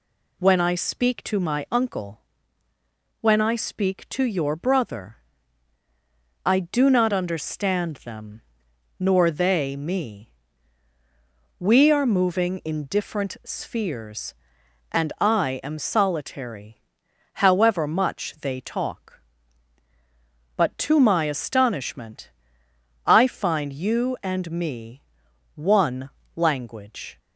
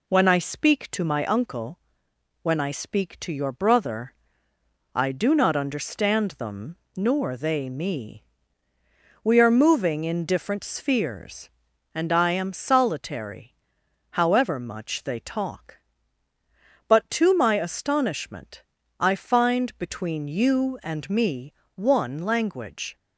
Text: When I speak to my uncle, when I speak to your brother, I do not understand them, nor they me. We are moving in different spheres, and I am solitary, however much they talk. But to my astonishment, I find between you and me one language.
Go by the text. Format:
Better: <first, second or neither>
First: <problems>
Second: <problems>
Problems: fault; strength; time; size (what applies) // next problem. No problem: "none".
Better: second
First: skips "between"; at 23.7 s // pauses between "me" and "one"; noticeable; at 25.0 s; 0.54 s long // pauses between "one" and "language"; slight; at 26.1 s; 0.24 s long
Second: pauses between "me" and "one"; slight; at 21.5 s; 0.24 s long